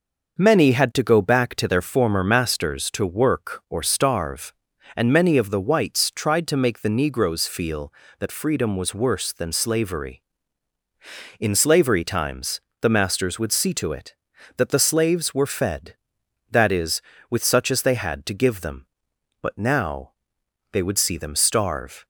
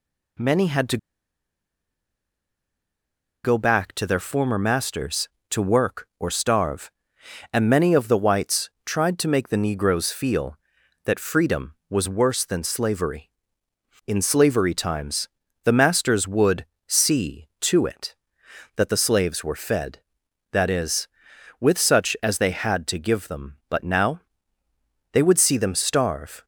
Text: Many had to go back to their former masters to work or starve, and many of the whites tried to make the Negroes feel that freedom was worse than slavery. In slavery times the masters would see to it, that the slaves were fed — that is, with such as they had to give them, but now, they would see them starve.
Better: first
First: pauses between "times" and "the"; slight; at 12.6 s; 0.20 s long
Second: pauses between "to" and "go"; strong; at 0.9 s; 2.4 s long // pauses between "times" and "the"; slight; at 15.2 s; 0.36 s long // pauses between "would" and "see"; slight; at 16.6 s; 0.24 s long

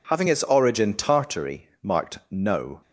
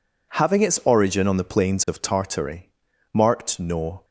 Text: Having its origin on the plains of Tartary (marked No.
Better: second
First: skips "on the plains of"; at 0.9 s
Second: none

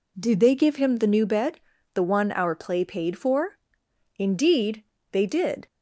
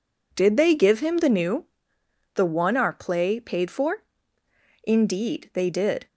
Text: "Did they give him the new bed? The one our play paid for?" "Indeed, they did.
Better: first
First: none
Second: skips "bed"; at 2.0 s

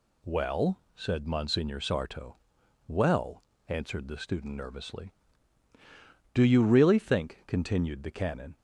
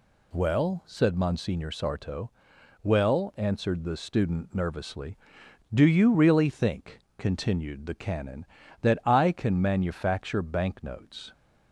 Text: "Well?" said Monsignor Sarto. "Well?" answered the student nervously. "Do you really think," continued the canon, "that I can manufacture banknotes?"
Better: second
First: stops before "that I can manufacture banknotes"; at 8.5 s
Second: none

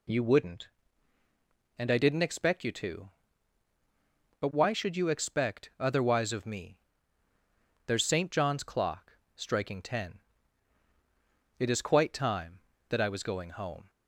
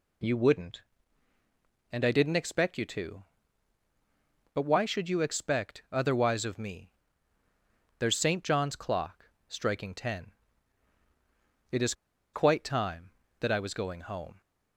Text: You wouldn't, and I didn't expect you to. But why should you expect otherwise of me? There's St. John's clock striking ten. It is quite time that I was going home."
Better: first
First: pauses between "clock" and "striking"; slight; at 9.1 s; 0.24 s long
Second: pauses between "clock" and "striking"; slight; at 9.2 s; 0.24 s long // pauses between "is" and "quite"; at 11.9 s; 0.41 s long

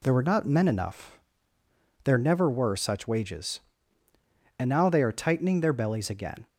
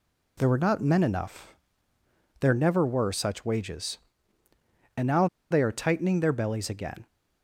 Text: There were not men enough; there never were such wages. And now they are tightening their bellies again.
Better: first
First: none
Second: pauses between "now" and "they"; slight; at 5.2 s; 0.24 s long

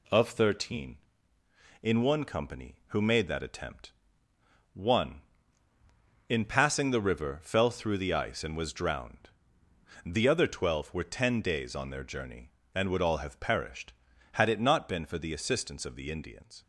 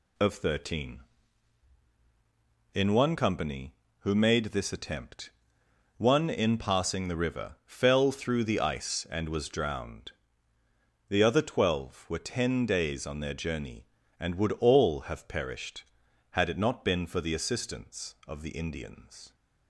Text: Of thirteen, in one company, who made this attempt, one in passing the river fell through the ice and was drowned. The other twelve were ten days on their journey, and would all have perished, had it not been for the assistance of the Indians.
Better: second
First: says "that" for "this"; at 3.2 s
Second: none

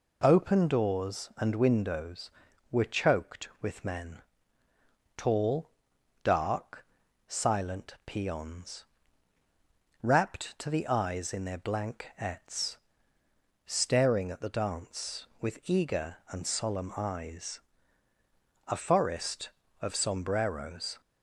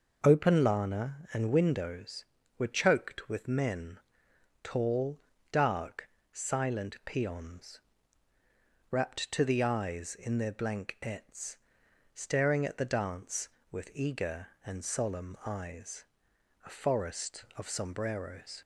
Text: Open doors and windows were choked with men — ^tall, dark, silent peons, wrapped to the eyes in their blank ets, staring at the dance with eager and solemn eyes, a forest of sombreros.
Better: first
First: none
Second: says "lana" for "doors"; at 0.6 s

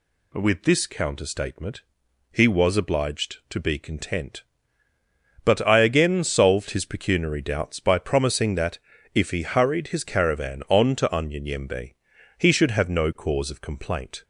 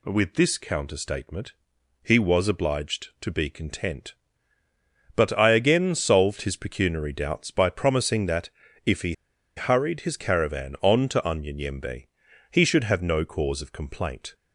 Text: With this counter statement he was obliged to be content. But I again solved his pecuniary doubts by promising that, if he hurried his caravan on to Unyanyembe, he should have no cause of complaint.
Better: first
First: pauses between "statement" and "he"; noticeable; at 1.8 s; 0.48 s long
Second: pauses between "statement" and "he"; noticeable; at 1.5 s; 0.48 s long // pauses between "he" and "hurried"; at 9.1 s; 0.43 s long

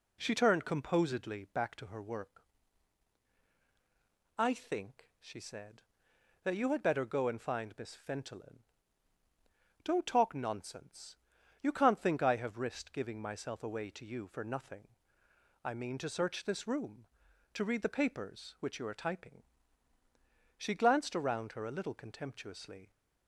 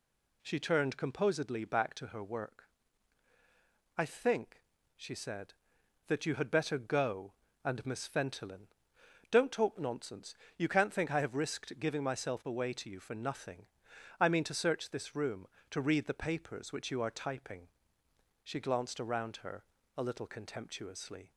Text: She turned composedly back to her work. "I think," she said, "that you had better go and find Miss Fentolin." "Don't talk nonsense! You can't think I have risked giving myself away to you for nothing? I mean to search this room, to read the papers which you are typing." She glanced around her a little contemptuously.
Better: first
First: none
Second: skips "find"; at 7.8 s // pauses between "her" and "a"; slight; at 19.6 s; 0.32 s long

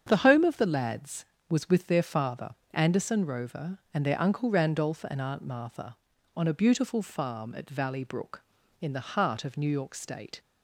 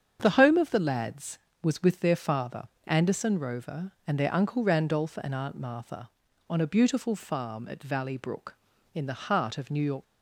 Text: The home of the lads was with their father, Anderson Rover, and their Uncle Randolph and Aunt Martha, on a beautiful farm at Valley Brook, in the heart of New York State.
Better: first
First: starts louder than the rest; strong; until 1.0 s; 8 dB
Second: starts louder than the rest; strong; until 1.2 s; 8 dB // stops before "State"; at 10.0 s

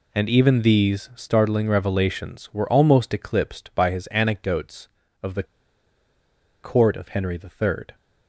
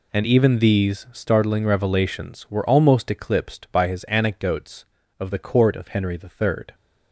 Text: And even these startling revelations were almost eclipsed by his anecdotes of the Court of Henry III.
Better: second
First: pauses between "the" and "Court"; at 5.4 s; 1.1 s long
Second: none

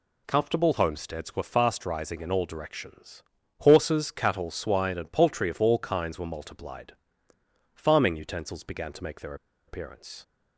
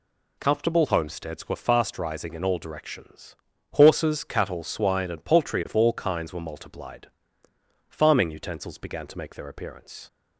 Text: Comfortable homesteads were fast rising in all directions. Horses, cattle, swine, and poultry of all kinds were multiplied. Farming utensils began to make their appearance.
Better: second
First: pauses between "their" and "appearance"; slight; at 9.3 s; 0.32 s long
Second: none

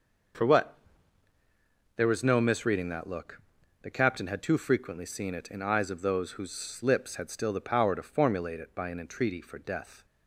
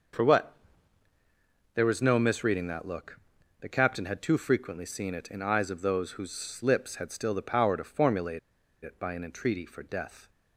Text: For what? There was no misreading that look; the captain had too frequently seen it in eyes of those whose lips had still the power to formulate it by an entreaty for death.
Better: first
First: starts louder than the rest; until 2.5 s; 6 dB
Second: starts louder than the rest; until 2.3 s; 6 dB // pauses between "formulate" and "it"; at 8.3 s; 0.43 s long

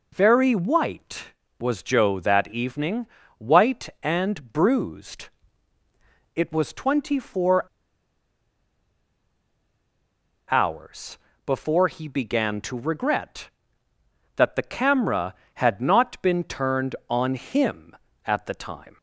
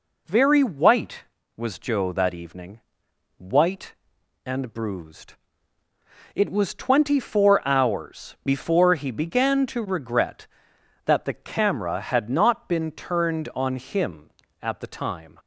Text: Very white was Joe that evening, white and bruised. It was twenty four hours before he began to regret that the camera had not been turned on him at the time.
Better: second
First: pauses between "four" and "hours"; strong; at 7.6 s; 2.8 s long // pauses between "hours" and "before"; slight; at 11.1 s; 0.30 s long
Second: none

